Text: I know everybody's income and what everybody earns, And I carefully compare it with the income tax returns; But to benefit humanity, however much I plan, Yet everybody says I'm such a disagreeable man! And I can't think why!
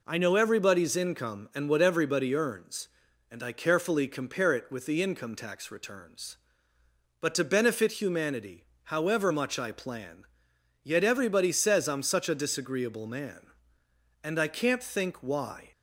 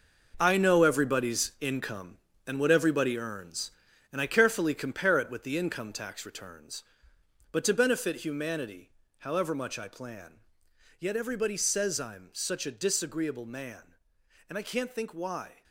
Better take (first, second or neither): first